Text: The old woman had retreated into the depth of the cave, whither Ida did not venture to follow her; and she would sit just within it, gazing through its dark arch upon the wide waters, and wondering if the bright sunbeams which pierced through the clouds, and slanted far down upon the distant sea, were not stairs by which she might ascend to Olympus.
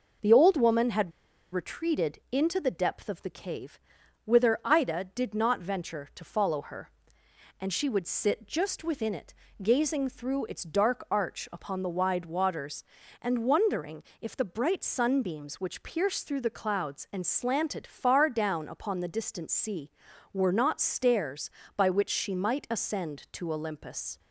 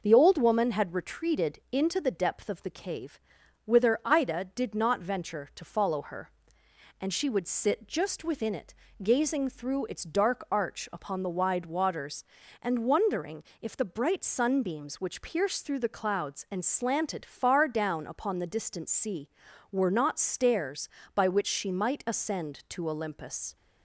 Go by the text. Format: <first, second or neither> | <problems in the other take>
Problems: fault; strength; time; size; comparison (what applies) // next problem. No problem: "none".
second | pauses between "had" and "retreated"; at 1.1 s; 0.41 s long // pauses between "wondering" and "if"; slight; at 14.0 s; 0.20 s long; slight in the second